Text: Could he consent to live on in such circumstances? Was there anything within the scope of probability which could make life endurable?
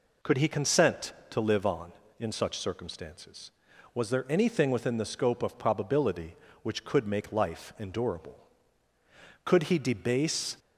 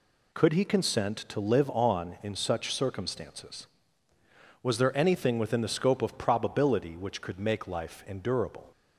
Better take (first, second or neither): second